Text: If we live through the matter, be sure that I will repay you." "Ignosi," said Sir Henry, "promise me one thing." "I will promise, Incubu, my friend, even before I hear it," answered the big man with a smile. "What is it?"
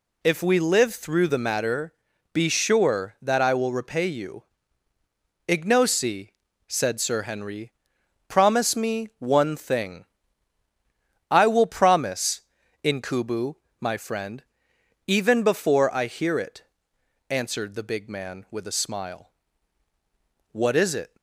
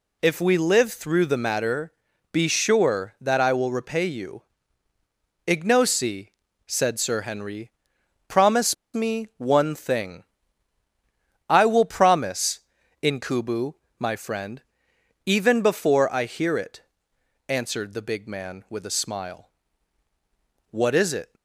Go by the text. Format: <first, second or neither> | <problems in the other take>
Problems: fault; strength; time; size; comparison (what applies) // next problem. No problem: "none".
first | pauses between "promise" and "me"; slight; at 8.7 s; 0.19 s long